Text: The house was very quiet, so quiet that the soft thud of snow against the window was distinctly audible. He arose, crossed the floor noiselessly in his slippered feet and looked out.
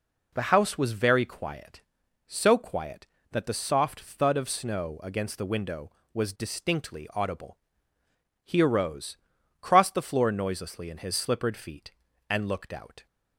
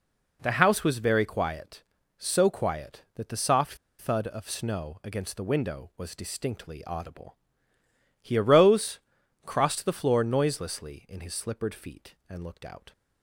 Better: first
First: none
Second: pauses between "soft" and "thud"; slight; at 3.7 s; 0.24 s long

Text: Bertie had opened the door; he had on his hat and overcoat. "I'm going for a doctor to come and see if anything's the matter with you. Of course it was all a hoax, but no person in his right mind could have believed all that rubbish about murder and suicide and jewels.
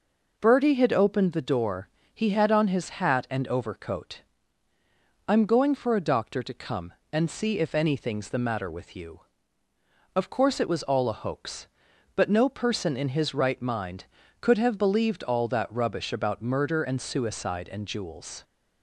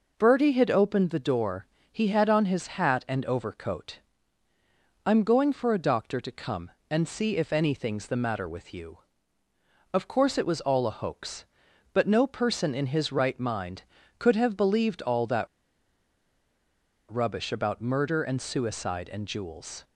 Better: first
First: none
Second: pauses between "that" and "rubbish"; strong; at 15.4 s; 1.6 s long

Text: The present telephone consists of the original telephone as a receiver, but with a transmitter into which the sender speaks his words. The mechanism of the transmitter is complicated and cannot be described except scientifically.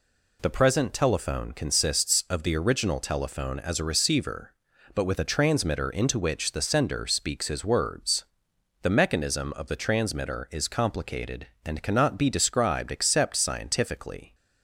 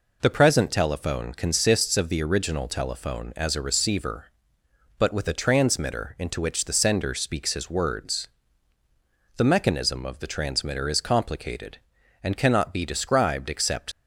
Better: first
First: none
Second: stops before "scientifically"; at 13.9 s

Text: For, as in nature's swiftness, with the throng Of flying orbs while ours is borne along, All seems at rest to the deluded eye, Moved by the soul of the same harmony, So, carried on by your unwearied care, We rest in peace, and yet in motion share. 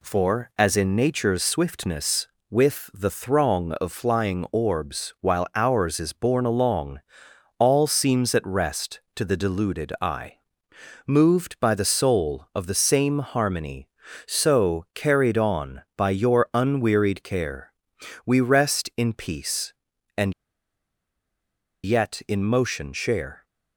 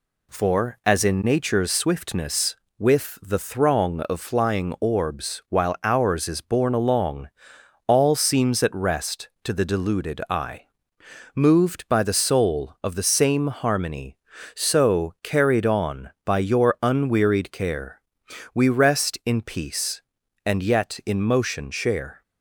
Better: second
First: pauses between "and" and "yet"; strong; at 20.3 s; 1.5 s long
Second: none

